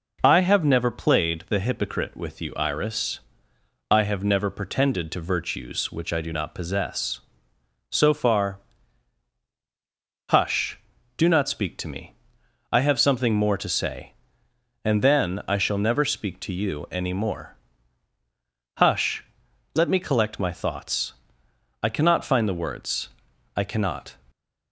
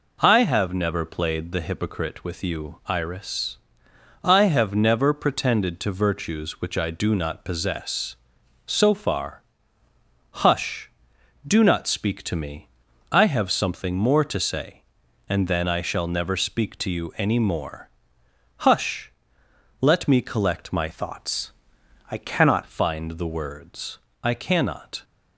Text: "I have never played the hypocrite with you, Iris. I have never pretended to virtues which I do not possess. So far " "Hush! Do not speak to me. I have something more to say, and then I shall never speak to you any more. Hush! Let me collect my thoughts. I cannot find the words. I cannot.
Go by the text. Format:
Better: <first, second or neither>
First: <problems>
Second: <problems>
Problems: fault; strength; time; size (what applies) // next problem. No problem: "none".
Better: first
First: none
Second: changes voice from "thoughts" to "cannot"; from 20.9 to 22.6 s; 1.7 s long